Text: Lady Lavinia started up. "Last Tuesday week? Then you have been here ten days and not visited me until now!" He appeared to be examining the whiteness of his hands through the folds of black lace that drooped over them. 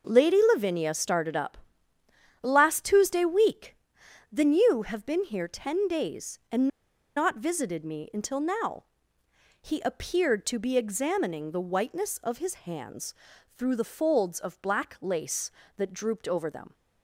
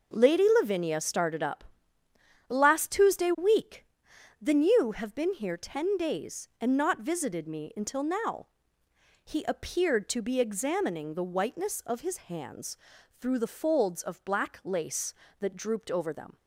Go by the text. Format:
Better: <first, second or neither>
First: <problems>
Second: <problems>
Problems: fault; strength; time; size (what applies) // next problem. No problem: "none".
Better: second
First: pauses between "and" and "not"; noticeable; at 6.6 s; 0.49 s long // pauses between "hands" and "through"; at 13.1 s; 0.42 s long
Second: pauses between "hands" and "through"; at 12.7 s; 0.42 s long